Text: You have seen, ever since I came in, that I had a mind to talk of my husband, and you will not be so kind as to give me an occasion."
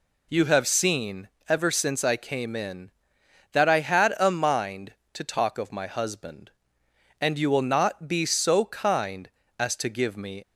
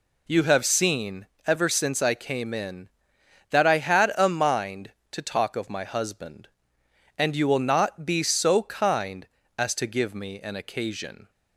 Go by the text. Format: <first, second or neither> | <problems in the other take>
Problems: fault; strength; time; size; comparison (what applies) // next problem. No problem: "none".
second | stops before "an occasion"; at 10.4 s